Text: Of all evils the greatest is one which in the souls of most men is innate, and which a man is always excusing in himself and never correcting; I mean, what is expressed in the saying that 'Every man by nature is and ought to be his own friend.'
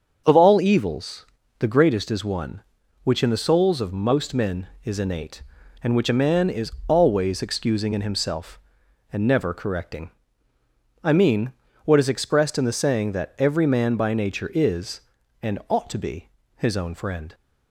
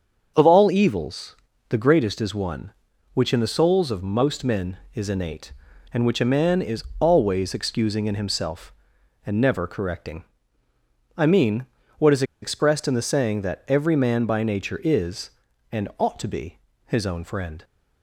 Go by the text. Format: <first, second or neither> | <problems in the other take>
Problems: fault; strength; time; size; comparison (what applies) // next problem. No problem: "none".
first | starts louder than the rest; until 1.3 s; 7 dB; also in the first // pauses between "evils" and "the"; slight; at 1.3 s; 0.32 s long; slight in the first // pauses between "is" and "always"; slight; at 6.8 s; 0.16 s long; slight in the first // pauses between "is" and "expressed"; slight; at 12.2 s; 0.18 s long // pauses between "be" and "his"; slight; at 16.5 s; 0.30 s long; slight in the first